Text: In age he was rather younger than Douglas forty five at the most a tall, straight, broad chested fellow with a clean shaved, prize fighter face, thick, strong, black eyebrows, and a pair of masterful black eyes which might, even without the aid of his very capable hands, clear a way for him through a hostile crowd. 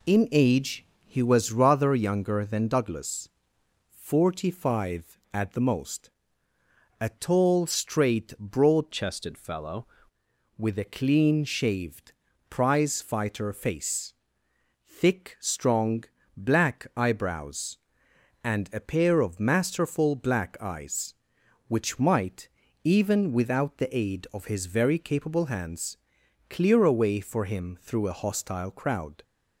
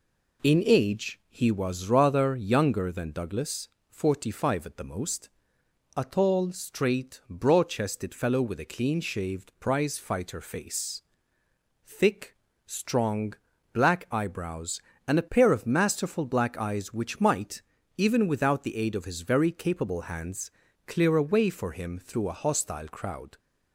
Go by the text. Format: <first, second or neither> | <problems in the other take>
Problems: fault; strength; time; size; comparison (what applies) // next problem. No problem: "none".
second | pauses between "age" and "he"; slight; at 0.8 s; 0.18 s long // pauses between "Douglas" and "forty"; noticeable; at 3.2 s; 0.60 s long; slight in the second // pauses between "most" and "a"; noticeable; at 6.0 s; 0.90 s long; noticeable in the second // changes voice from "chested" to "fellow"; from 8.9 to 9.8 s; 0.9 s long